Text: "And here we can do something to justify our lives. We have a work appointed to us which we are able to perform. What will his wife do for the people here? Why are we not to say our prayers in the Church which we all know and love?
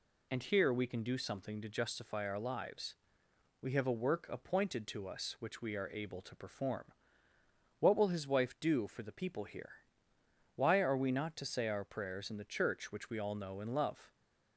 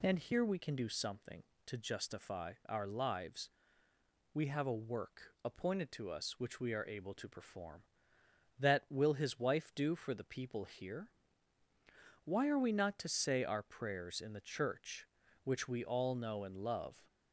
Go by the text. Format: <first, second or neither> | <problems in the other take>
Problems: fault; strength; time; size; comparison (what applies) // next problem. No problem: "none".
first | says "That" for "What"; at 8.5 s